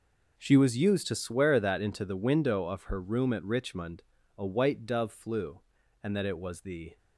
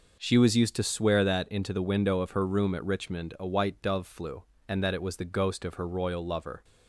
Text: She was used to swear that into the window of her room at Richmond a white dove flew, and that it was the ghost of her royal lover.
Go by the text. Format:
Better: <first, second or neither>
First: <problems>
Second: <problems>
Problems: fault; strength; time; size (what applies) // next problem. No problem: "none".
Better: second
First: pauses between "Richmond" and "a"; slight; at 4.0 s; 0.34 s long // stops before "ghost of her royal lover"; at 6.9 s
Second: none